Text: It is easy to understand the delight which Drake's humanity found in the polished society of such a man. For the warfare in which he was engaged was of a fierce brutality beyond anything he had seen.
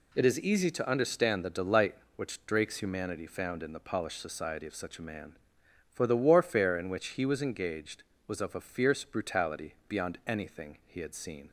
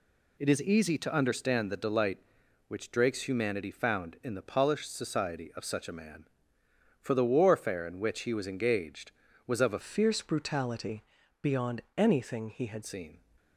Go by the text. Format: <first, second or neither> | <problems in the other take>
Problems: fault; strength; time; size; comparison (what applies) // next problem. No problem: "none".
first | changes voice from "fierce" to "had"; from 9.8 to 12.8 s; 3.0 s long // pauses between "brutality" and "beyond"; at 11.0 s; 0.40 s long // pauses between "beyond" and "anything"; slight; at 11.8 s; 0.16 s long